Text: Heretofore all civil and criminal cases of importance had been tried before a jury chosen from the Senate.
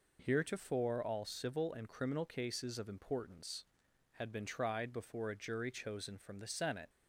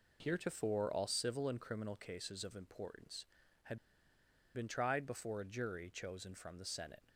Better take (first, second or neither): first